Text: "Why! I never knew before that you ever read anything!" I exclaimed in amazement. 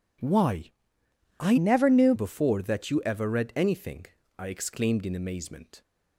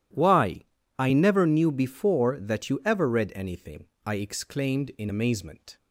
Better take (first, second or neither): second